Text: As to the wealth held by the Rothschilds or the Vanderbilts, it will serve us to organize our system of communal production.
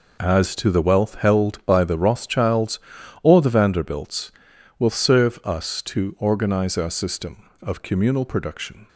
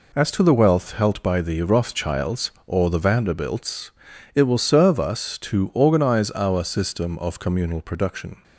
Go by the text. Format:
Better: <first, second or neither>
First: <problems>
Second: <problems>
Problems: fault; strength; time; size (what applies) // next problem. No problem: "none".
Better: second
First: skips "it"; at 4.5 s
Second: none